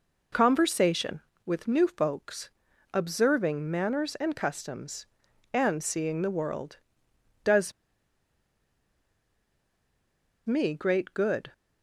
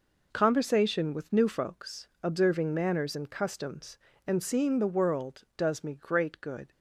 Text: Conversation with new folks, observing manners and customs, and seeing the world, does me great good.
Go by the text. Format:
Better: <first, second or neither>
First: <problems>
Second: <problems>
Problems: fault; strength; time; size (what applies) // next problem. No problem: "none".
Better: second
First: pauses between "does" and "me"; strong; at 7.7 s; 2.7 s long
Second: none